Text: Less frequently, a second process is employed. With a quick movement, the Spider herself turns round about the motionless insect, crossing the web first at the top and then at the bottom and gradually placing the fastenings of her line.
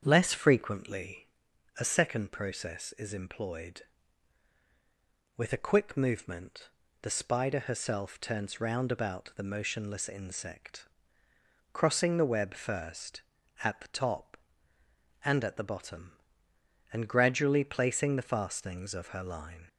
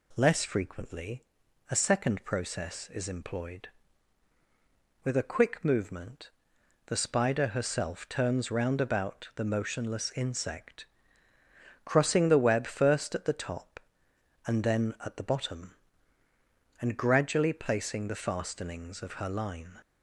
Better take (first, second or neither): second